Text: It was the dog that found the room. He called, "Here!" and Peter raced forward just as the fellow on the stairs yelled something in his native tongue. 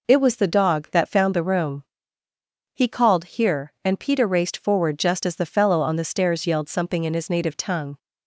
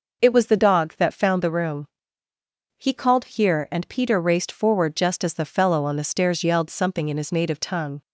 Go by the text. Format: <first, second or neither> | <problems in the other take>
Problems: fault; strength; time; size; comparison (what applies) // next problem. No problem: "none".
neither | none